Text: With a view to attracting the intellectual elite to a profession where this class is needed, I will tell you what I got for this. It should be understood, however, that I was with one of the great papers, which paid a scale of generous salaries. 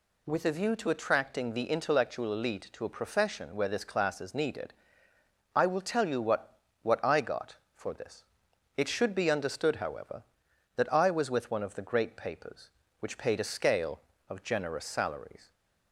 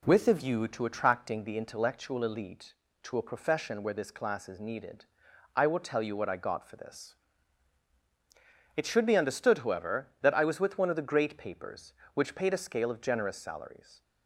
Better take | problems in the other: second | says "what" twice; at 6.8 s

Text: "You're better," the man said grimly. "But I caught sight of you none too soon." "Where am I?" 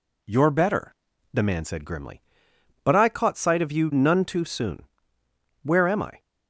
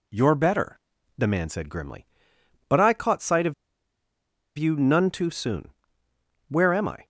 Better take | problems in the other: first | pauses between "of" and "you"; at 3.5 s; 1.0 s long

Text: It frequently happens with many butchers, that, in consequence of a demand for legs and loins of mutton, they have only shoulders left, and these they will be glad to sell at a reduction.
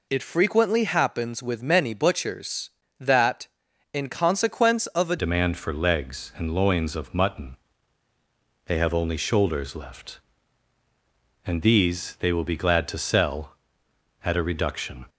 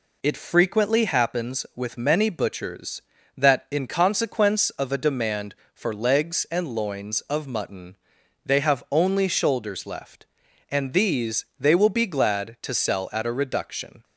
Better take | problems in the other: second | changes voice at "demand"; from 5.1 s on; 9.9 s long

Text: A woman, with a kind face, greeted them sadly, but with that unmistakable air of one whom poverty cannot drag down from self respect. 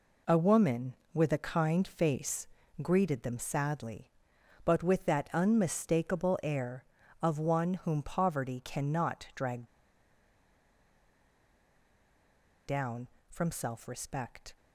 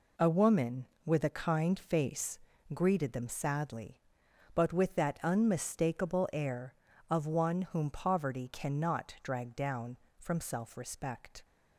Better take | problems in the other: second | pauses between "drag" and "down"; strong; at 9.6 s; 3.0 s long

